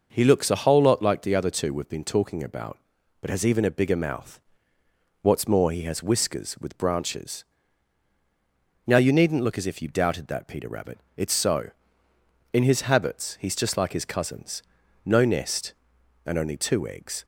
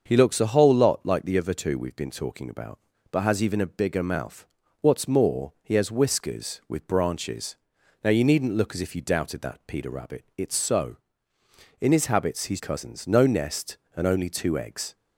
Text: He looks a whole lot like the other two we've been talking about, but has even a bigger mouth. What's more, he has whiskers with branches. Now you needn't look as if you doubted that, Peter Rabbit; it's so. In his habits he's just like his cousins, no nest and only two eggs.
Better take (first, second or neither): first